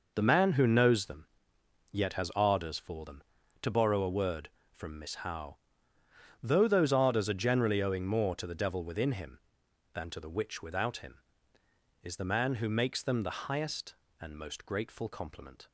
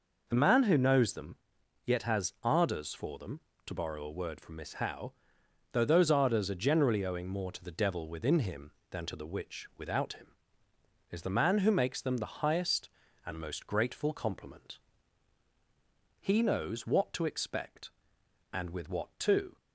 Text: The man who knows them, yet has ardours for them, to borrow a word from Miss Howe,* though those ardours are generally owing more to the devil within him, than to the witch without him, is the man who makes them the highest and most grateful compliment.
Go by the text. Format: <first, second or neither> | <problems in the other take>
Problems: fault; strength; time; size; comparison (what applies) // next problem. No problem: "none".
first | goes on to say "He knows what to expect and with what to"; strong; from 16.1 s on; 3.3 s long